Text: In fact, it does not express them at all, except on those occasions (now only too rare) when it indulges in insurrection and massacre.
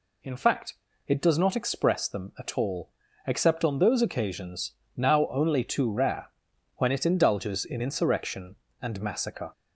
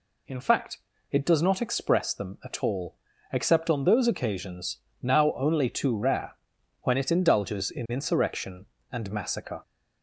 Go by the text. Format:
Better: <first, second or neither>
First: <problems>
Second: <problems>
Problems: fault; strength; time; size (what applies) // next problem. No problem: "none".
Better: neither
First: none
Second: none